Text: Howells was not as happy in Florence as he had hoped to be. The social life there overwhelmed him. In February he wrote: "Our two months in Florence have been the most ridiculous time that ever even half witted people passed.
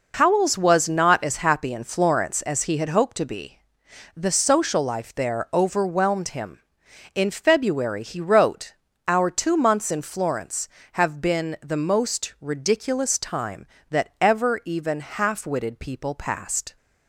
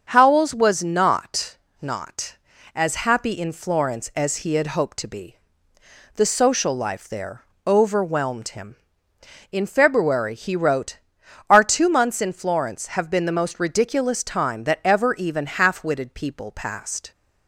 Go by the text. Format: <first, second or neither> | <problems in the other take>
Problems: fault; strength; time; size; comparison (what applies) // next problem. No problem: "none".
first | starts louder than the rest; until 1.1 s; 7 dB // says "not" twice; at 1.8 s // pauses between "there" and "overwhelmed"; slight; at 7.4 s; 0.22 s long